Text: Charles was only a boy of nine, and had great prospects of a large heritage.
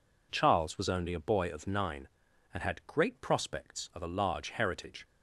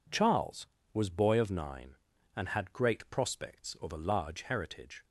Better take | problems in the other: first | skips "only a"; at 1.0 s

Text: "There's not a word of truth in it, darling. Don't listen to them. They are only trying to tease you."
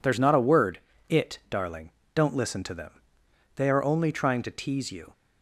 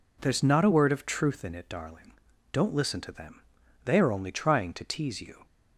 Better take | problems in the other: second | skips "of truth in"; at 0.9 s

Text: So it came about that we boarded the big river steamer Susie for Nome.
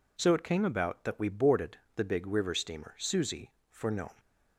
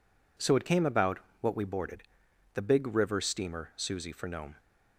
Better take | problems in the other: first | says "what" for "that"; at 1.3 s // pauses between "boarded" and "the"; noticeable; at 2.0 s; 0.50 s long; slight in the first

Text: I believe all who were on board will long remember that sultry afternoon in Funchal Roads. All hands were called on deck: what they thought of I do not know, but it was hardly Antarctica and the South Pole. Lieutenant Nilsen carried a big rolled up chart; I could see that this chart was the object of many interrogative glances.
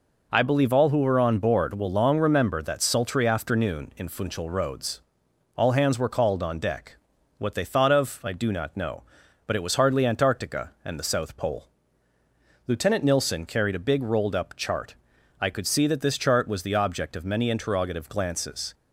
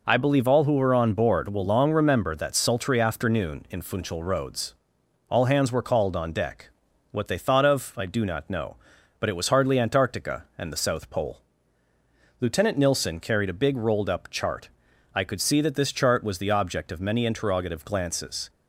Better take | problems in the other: neither | none

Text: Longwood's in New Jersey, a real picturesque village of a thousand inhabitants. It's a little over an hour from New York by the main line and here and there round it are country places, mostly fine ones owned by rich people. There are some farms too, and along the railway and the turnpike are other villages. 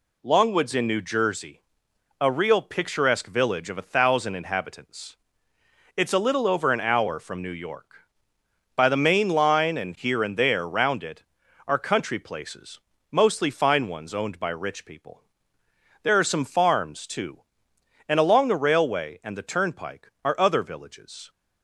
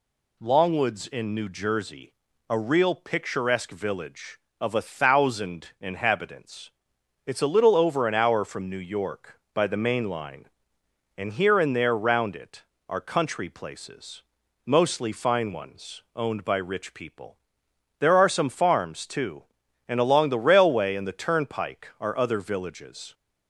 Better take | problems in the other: neither | none

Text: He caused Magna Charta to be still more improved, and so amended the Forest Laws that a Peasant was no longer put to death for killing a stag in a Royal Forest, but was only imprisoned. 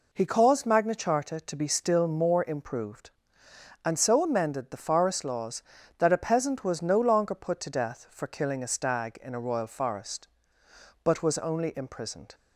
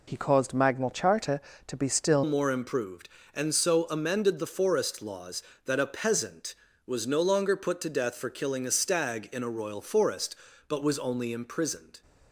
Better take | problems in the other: first | changes voice at "more"; from 2.2 s on; 9.8 s long

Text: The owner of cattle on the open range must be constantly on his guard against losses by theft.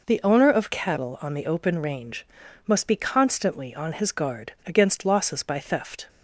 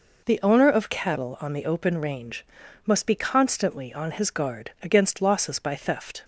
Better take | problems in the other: neither | pauses between "range" and "must"; the same in both

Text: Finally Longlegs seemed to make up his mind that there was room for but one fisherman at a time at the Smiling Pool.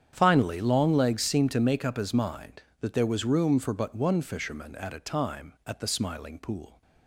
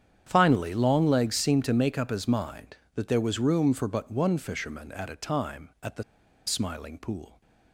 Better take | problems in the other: first | starts louder than the rest; strong; until 1.2 s; 9 dB; strong in the first // pauses between "the" and "Smiling"; at 6.0 s; 0.43 s long

